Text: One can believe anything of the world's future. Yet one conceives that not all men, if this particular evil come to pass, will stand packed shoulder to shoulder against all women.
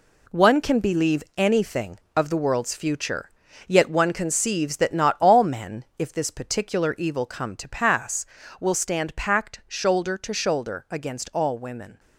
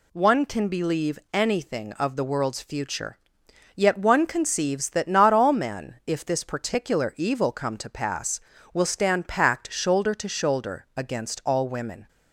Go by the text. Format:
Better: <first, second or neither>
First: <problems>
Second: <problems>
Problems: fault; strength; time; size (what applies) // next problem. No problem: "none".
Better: second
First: gets quieter; strong; throughout; 8.5 dB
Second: none